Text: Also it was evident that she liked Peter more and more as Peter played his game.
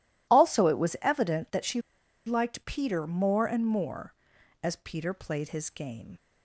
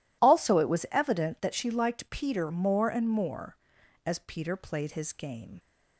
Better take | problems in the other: second | pauses between "she" and "liked"; noticeable; at 1.7 s; 0.46 s long

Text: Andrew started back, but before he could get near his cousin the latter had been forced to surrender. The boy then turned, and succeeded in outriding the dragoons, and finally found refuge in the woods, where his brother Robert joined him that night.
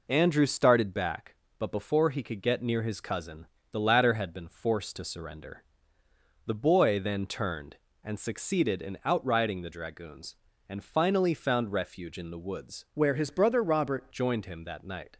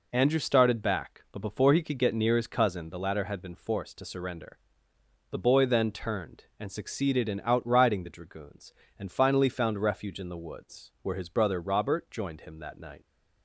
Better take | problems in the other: second | pauses between "cousin" and "the"; slight; at 3.4 s; 0.24 s long // changes voice from "where" to "Robert"; from 12.9 to 14.1 s; 1.2 s long

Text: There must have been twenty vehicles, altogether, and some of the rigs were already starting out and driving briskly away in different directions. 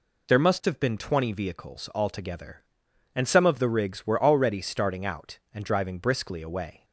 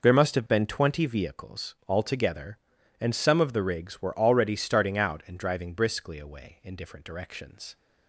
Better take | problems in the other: second | stops before "in different directions"; at 6.8 s

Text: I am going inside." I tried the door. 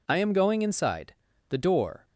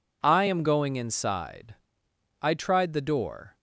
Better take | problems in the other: second | skips "I tried"; at 1.3 s

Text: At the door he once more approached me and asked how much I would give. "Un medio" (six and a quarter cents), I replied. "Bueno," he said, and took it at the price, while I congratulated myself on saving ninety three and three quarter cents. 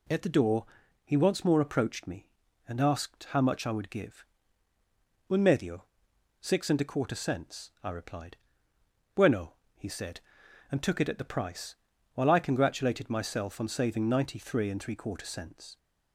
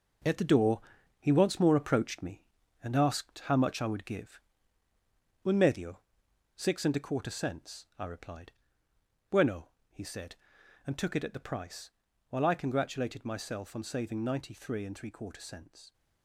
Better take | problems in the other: first | gets quieter; strong; throughout; 8 dB // pauses between "door" and "he"; at 0.8 s; 0.38 s long; also in the first

